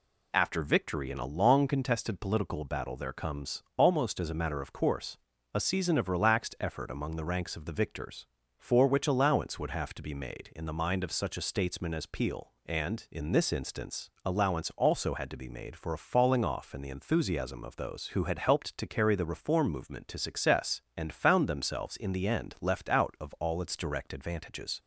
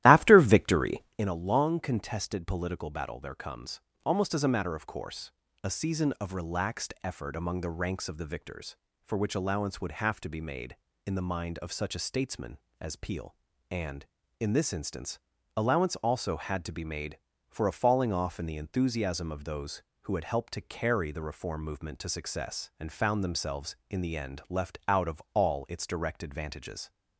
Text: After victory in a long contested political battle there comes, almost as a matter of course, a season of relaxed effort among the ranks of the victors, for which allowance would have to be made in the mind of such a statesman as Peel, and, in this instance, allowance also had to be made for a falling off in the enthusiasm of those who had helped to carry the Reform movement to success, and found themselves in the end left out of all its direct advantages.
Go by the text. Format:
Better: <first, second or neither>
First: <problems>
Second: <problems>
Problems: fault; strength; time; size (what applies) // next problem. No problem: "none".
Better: first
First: none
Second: starts louder than the rest; strong; until 1.3 s; 14.5 dB